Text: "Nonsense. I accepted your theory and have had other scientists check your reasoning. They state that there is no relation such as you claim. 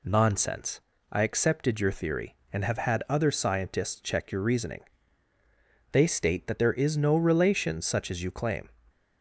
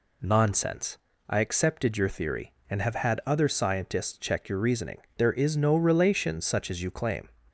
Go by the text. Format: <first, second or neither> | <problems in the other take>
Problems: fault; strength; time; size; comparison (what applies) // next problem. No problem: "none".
first | skips "They state that"; at 5.0 s